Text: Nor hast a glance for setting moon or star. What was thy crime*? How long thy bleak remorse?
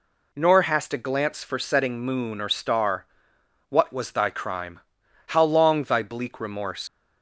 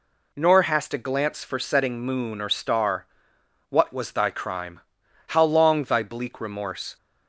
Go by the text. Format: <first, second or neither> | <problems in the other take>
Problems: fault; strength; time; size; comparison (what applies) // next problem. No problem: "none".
second | leaves "remorse" unfinished; at 6.8 s; 85 ms